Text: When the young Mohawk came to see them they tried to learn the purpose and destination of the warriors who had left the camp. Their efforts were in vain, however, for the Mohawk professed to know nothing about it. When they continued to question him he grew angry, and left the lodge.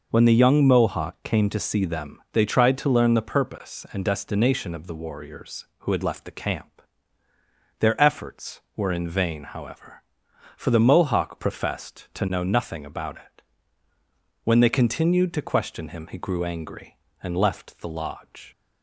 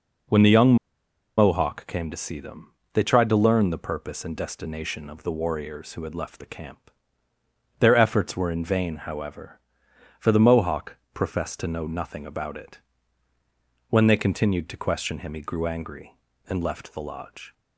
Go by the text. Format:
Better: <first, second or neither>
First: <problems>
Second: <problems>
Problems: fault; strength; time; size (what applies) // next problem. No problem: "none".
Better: first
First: none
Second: pauses between "young" and "Mohawk"; noticeable; at 0.7 s; 0.62 s long // pauses between "them" and "they"; slight; at 2.7 s; 0.22 s long // pauses between "Mohawk" and "professed"; slight; at 10.9 s; 0.16 s long